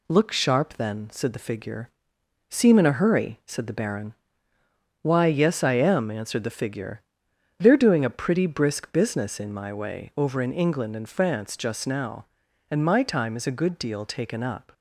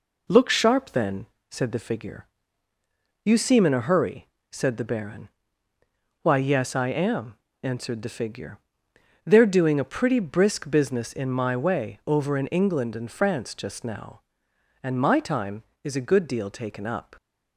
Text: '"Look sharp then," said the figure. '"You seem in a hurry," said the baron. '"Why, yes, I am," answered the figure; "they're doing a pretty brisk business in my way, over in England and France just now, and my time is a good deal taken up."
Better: second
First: skips "You"; at 2.1 s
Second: none

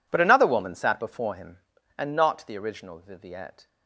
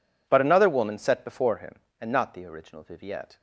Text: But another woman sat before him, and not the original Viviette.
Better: first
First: none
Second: says "set" for "sat"; at 0.9 s

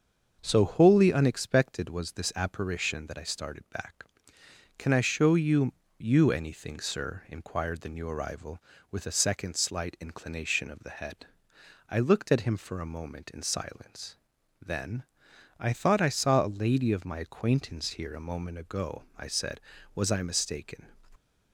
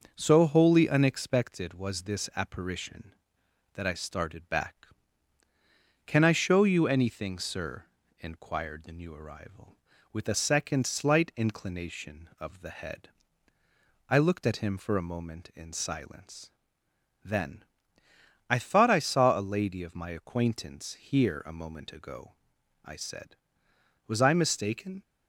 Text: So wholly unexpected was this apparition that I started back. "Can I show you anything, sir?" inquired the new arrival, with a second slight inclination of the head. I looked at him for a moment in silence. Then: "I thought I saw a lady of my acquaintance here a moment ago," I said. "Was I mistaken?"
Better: second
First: starts louder than the rest; until 1.4 s; 6.5 dB // says "you" twice; at 6.0 s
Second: none

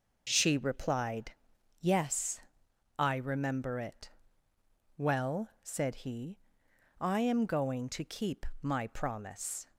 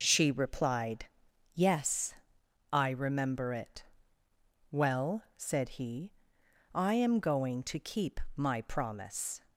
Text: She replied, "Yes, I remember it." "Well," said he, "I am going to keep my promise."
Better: neither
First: pauses between "keep" and "my"; slight; at 8.4 s; 0.16 s long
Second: pauses between "keep" and "my"; slight; at 8.1 s; 0.18 s long

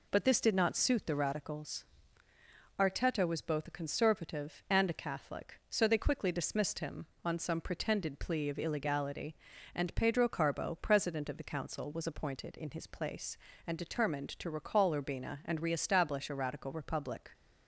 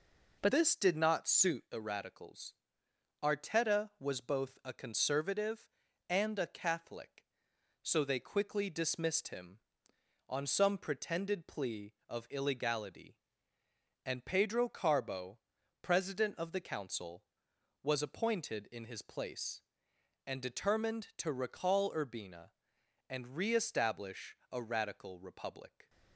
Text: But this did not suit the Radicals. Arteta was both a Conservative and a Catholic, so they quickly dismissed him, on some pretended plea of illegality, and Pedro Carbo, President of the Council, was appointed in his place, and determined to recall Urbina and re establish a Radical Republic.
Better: first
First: none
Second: changes voice at "this"; from 0.5 s on; 25.3 s long

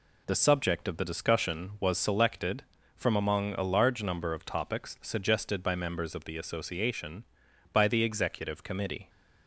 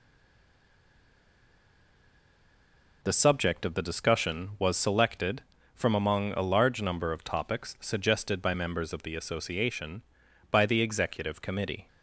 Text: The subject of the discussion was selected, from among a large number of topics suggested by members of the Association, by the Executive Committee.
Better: first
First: none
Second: stays silent before the first word; strong; until 3.0 s; 3.0 s long

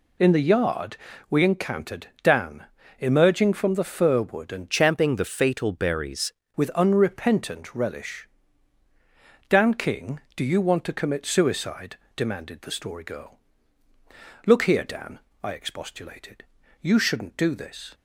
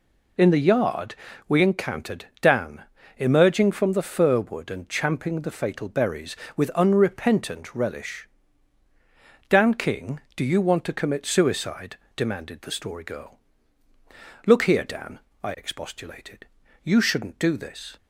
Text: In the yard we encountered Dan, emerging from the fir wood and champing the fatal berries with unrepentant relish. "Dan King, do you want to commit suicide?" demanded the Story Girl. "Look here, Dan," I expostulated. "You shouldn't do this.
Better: second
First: pauses between "yard" and "we"; slight; at 0.9 s; 0.34 s long // changes voice from "champing" to "berries"; from 4.7 to 6.3 s; 1.6 s long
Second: pauses between "yard" and "we"; slight; at 1.1 s; 0.34 s long

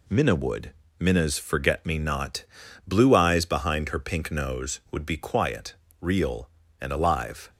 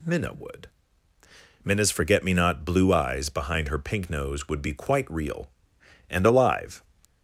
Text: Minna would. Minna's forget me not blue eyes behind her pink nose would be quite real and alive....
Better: second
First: pauses between "not" and "blue"; at 2.4 s; 0.42 s long // says "quiet" for "quite"; at 5.1 s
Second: none

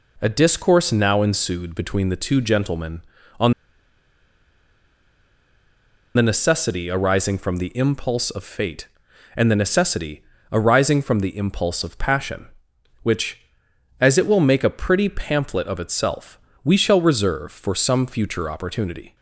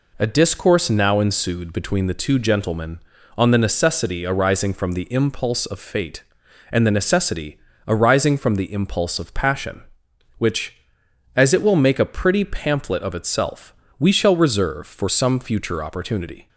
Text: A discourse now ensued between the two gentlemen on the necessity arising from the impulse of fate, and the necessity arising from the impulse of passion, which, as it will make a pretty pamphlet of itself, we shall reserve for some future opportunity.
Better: second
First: pauses between "on" and "the"; strong; at 3.5 s; 2.6 s long // pauses between "necessity" and "arising"; slight; at 10.2 s; 0.30 s long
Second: pauses between "necessity" and "arising"; slight; at 7.5 s; 0.30 s long

